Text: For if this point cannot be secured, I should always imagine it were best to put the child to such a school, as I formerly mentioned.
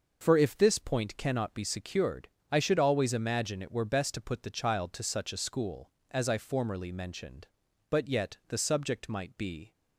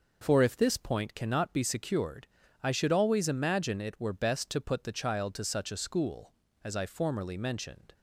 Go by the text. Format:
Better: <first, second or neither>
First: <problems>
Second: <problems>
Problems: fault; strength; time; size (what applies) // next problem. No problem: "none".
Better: second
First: goes on to say "But yet the subject might be"; strong; from 7.8 s on; 1.8 s long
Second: none